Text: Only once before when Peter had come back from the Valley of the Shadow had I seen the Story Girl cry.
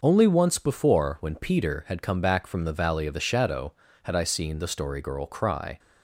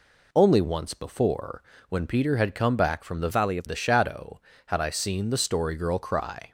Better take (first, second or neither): first